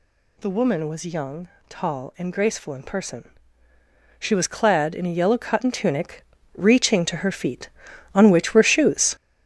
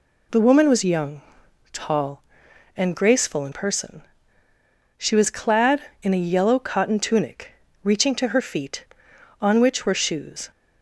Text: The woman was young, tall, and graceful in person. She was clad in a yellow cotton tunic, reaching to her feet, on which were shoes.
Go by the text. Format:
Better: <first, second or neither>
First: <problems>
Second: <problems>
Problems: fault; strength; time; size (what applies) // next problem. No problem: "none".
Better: second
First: gets louder; strong; throughout; 8 dB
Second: none